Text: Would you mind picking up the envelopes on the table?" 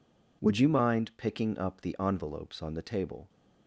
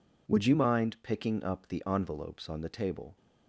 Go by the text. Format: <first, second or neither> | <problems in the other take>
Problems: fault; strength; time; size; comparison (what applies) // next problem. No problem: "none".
neither | none